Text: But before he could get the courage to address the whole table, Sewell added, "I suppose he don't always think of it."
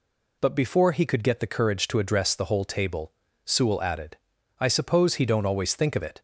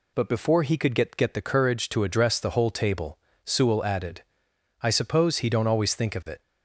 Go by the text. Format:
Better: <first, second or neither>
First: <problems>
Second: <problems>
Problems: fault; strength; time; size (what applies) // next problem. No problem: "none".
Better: first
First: none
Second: says "get" twice; at 1.1 s